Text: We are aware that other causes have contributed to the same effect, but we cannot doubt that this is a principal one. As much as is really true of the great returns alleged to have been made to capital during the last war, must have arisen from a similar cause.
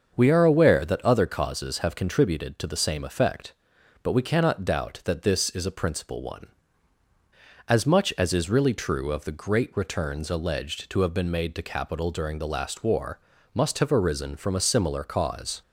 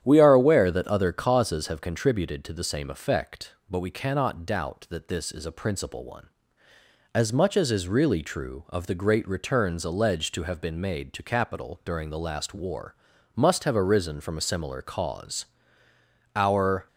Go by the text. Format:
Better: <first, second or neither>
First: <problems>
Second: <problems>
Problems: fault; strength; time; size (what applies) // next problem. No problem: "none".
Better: first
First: starts louder than the rest; until 1.1 s; 6.5 dB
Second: starts louder than the rest; strong; until 1.0 s; 9.5 dB // goes on to say "Our"; from 16.3 s on; 0.52 s long